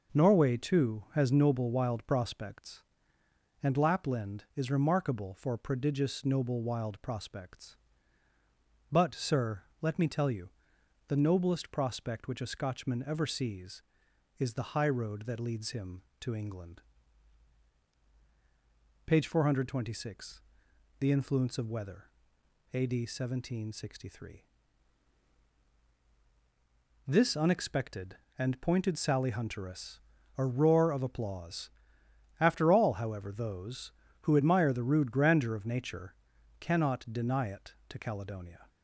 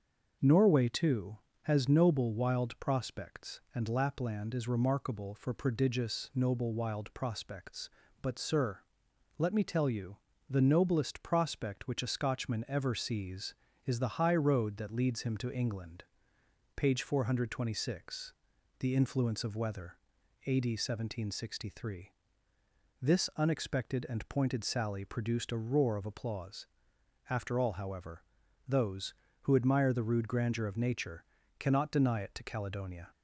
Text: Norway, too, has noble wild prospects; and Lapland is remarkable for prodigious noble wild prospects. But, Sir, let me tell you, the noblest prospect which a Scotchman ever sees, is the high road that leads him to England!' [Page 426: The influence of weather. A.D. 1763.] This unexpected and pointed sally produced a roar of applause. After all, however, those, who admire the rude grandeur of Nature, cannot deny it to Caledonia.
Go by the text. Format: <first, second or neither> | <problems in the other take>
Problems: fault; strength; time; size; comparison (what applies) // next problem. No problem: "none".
second | starts louder than the rest; noticeable; until 1.2 s; 6 dB; noticeable in the second // says "hunteress" for "produced"; at 29.3 s